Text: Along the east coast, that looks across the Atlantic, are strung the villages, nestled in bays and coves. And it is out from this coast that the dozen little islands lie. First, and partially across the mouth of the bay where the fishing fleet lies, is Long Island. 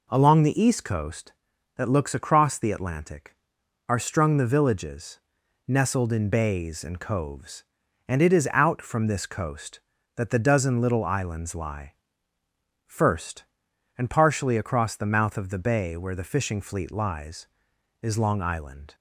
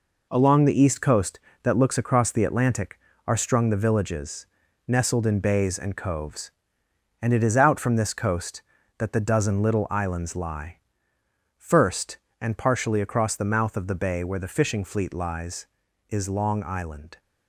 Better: first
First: none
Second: gets quieter; throughout; 7 dB

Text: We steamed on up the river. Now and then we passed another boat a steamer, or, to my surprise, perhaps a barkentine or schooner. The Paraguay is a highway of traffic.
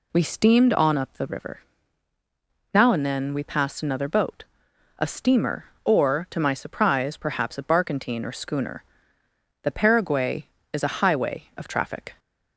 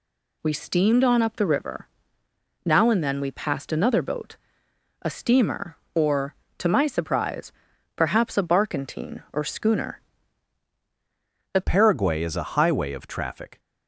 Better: first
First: pauses between "boat" and "a"; noticeable; at 4.4 s; 0.56 s long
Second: pauses between "boat" and "a"; noticeable; at 4.3 s; 0.66 s long // changes voice at "Paraguay"; from 11.6 s on; 1.9 s long

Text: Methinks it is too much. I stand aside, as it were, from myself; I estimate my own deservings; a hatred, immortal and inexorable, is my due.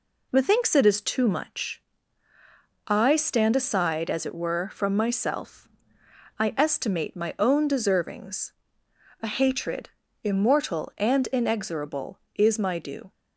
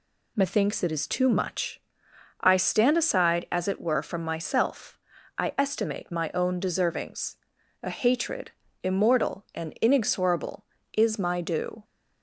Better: neither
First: none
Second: none

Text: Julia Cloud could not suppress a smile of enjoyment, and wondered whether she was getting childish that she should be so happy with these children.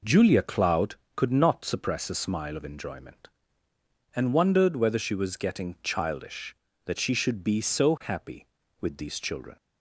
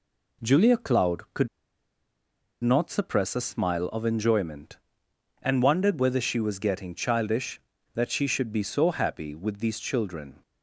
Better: first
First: none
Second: pauses between "could" and "not"; at 1.4 s; 1.1 s long

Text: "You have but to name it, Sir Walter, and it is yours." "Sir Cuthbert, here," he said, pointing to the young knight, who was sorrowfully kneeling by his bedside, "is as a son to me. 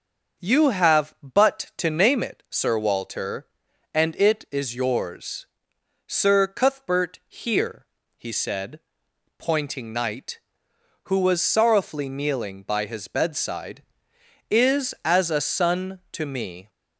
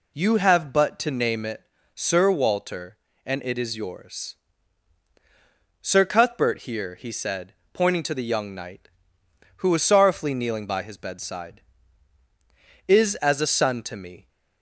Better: second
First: starts louder than the rest; until 1.4 s; 6.5 dB // skips "to the young"; at 9.9 s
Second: none

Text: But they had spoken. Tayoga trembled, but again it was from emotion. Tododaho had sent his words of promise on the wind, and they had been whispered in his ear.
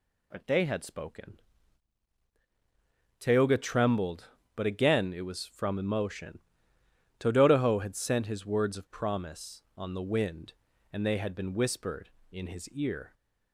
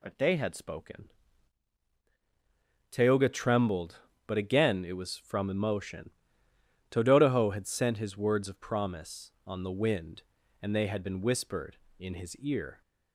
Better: neither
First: none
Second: none

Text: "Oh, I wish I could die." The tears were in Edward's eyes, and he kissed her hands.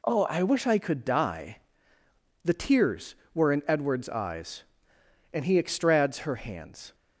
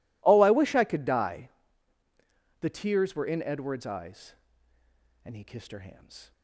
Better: second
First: says "extrads" for "kissed"; at 5.5 s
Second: none

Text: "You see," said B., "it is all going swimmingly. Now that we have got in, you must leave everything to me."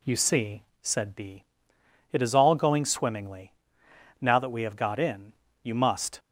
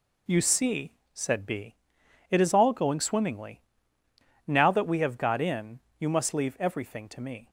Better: second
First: stops before "leave everything to me"; at 6.1 s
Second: none

